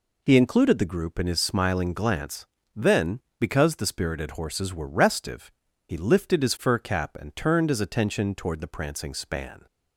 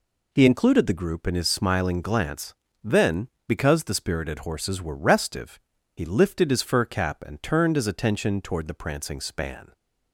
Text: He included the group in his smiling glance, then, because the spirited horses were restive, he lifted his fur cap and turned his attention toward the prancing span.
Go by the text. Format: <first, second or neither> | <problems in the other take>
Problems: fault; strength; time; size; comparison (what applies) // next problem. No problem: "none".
neither | none